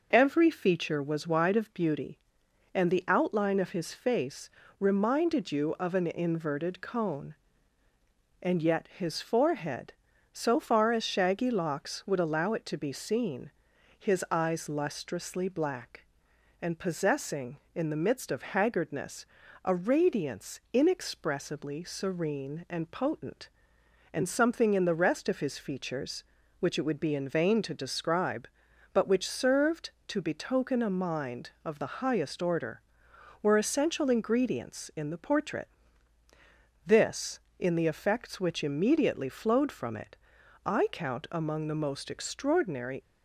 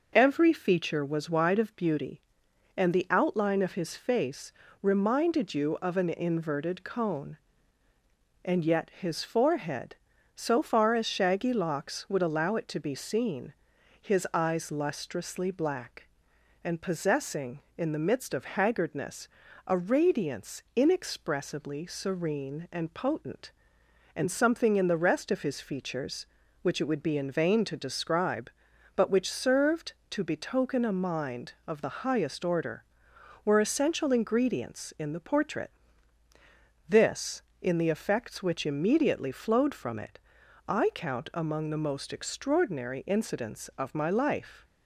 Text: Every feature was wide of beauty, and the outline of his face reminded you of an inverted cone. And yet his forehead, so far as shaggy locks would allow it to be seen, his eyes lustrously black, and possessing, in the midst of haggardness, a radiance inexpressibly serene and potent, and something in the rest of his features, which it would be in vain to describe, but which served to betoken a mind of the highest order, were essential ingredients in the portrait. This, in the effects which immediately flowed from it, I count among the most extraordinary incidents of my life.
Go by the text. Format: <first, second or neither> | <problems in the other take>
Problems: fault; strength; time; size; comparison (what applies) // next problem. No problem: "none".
second | pauses between "face" and "reminded"; slight; at 4.4 s; 0.28 s long; slight in the second // stops before "incidents of my life"; at 43.0 s